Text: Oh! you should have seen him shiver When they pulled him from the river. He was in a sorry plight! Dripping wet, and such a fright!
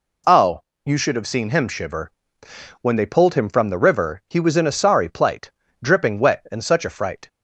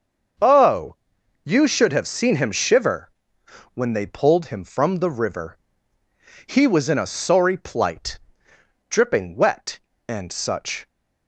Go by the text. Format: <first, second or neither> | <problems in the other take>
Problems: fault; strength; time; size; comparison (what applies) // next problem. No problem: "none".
first | starts louder than the rest; until 1.8 s; 6.5 dB // pauses between "shiver" and "When"; noticeable; at 3.1 s; 0.62 s long; noticeable in the first // stops before "a fright"; at 10.8 s